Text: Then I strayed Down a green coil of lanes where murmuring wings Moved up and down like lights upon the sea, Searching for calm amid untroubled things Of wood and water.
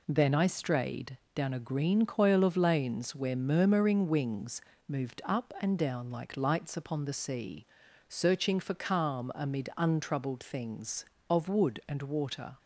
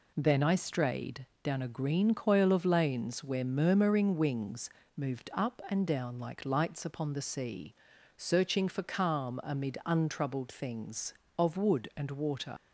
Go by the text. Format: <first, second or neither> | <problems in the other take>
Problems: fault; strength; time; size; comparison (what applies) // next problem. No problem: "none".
first | pauses between "strayed" and "Down"; slight; at 1.2 s; 0.18 s long; slight in the first // pauses between "wings" and "Moved"; slight; at 4.6 s; 0.26 s long; slight in the first // leaves "water" unfinished; at 12.5 s; 100 ms